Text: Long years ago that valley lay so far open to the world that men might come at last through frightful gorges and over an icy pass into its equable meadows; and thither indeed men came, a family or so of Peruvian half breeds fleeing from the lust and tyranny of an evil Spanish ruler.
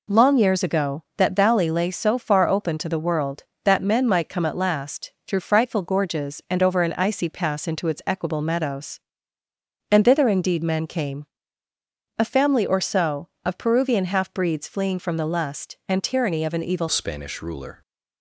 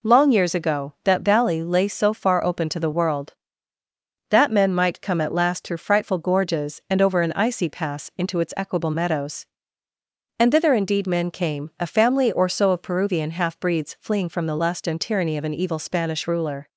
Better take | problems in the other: second | pauses between "last" and "through"; slight; at 5.1 s; 0.16 s long // changes voice at "Spanish"; from 16.8 s on; 1.0 s long

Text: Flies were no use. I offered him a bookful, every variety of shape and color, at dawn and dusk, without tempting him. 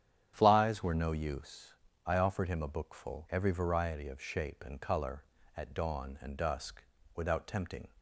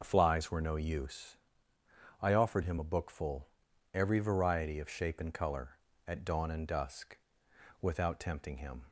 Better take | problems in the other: second | starts louder than the rest; strong; until 1.3 s; 9.5 dB // stops before "him"; at 7.9 s

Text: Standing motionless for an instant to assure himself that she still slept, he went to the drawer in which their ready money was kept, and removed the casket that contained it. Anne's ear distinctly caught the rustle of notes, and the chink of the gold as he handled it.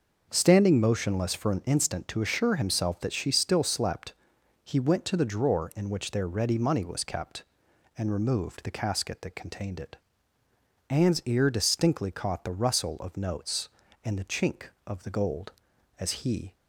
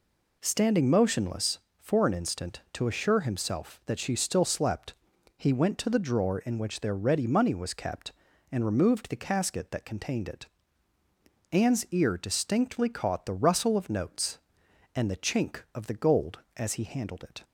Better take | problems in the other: second | stops before "handled it"; at 16.5 s

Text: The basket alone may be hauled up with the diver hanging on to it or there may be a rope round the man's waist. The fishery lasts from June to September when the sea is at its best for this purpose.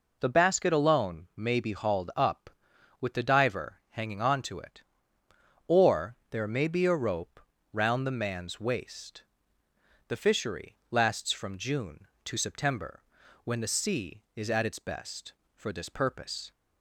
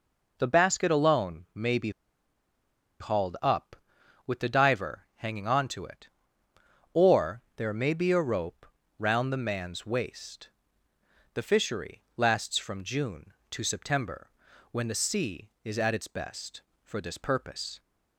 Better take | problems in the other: first | pauses between "be" and "hauled"; at 1.9 s; 1.1 s long // pauses between "rope" and "round"; slight; at 8.6 s; 0.32 s long; slight in the first // pauses between "fishery" and "lasts"; slight; at 12.0 s; 0.16 s long; slight in the first // pauses between "September" and "when"; at 14.2 s; 0.42 s long; also in the first

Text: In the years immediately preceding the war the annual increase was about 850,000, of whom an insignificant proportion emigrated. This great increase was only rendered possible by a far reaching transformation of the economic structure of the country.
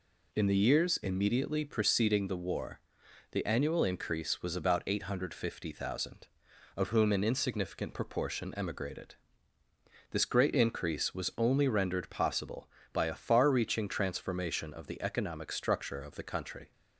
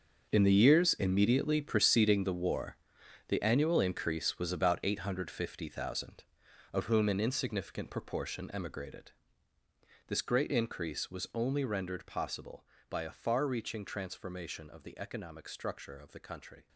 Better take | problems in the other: first | gets quieter; strong; throughout; 14.5 dB // pauses between "war" and "the"; noticeable; at 2.7 s; 0.52 s long; noticeable in the first

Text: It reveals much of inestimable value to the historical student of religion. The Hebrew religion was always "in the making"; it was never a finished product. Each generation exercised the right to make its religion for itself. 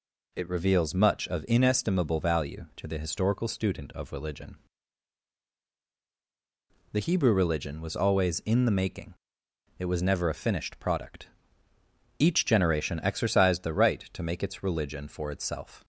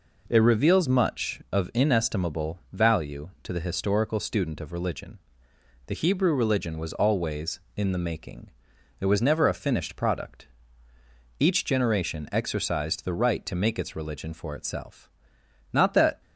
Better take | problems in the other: first | goes on to say "Not that"; slight; from 15.7 s on; 0.48 s long

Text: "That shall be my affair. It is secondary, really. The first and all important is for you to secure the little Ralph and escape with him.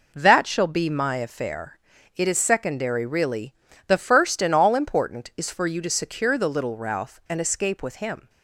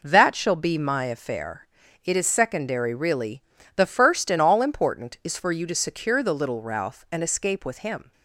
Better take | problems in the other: neither | none

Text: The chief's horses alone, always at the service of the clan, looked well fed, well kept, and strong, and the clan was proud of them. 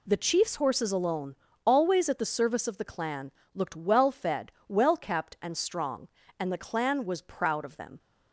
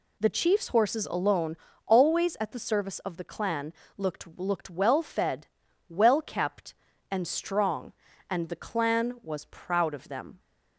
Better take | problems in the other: first | says "looked" twice; at 4.3 s

